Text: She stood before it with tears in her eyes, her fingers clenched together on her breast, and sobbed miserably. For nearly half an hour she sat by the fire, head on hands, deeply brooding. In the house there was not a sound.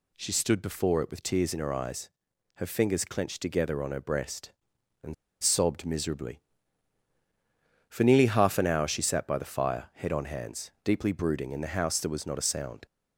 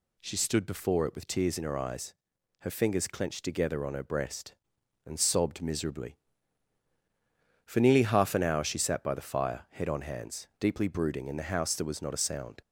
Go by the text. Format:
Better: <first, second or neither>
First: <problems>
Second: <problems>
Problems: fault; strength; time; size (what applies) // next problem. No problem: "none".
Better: second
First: pauses between "and" and "sobbed"; slight; at 5.1 s; 0.28 s long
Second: none